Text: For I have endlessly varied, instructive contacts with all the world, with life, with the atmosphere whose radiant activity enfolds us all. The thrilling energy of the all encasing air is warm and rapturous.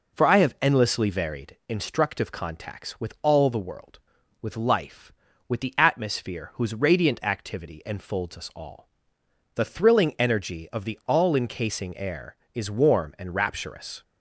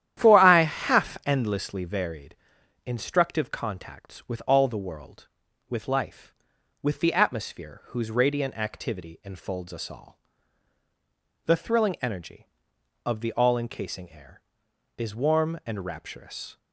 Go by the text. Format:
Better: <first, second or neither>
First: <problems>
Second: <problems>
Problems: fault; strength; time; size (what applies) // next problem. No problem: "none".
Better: first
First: none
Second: starts louder than the rest; strong; until 1.2 s; 11 dB // says "half" for "have"; at 0.6 s